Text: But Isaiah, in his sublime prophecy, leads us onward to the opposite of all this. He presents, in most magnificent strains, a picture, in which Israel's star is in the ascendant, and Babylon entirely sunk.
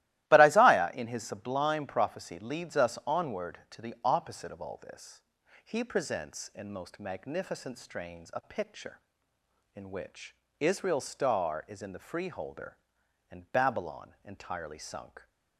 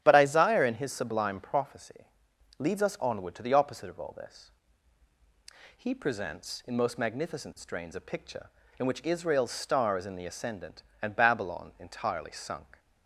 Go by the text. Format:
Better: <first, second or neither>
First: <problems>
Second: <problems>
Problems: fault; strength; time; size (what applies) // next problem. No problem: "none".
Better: second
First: starts louder than the rest; strong; until 1.3 s; 16 dB // pauses between "which" and "Israel's"; slight; at 10.3 s; 0.26 s long // says "freeholder" for "ascendant"; at 11.9 s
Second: starts louder than the rest; strong; until 1.0 s; 11 dB